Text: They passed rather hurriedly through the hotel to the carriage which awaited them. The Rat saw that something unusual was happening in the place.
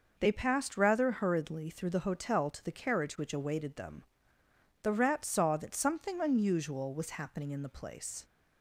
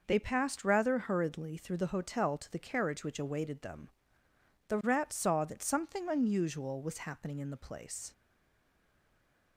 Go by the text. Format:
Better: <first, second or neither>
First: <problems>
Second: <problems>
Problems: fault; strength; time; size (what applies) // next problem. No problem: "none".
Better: first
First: none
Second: stays silent after the last word; noticeable; from 8.1 s on; 1.4 s long